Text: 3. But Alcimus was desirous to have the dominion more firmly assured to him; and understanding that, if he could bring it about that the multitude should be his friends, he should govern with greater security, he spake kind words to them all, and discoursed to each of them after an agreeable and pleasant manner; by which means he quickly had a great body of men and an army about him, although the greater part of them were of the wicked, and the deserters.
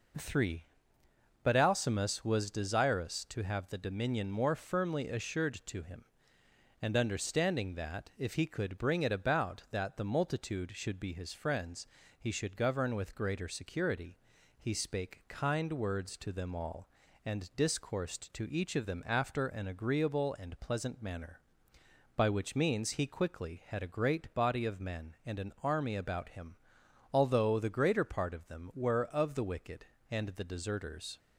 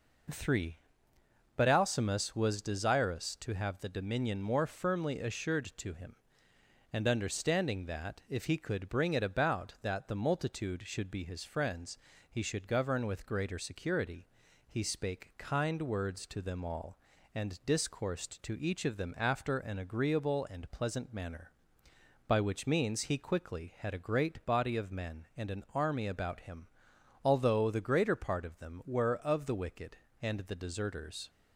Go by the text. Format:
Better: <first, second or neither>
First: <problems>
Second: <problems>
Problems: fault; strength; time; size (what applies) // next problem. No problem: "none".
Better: neither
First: none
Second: none